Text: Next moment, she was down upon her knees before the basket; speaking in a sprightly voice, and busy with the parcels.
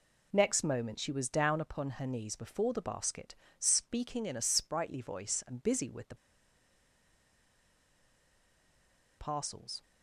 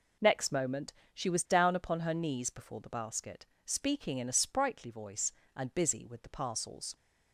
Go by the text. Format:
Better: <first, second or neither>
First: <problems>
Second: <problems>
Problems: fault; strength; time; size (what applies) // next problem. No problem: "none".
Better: second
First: pauses between "the" and "parcels"; strong; at 6.1 s; 3.0 s long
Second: none